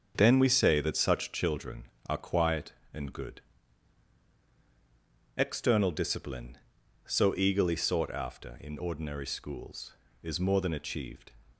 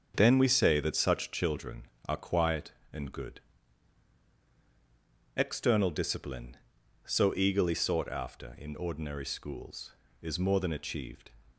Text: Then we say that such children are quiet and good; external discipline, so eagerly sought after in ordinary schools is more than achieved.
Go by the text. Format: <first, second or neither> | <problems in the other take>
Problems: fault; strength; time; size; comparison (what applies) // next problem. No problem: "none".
neither | starts louder than the rest; the same in both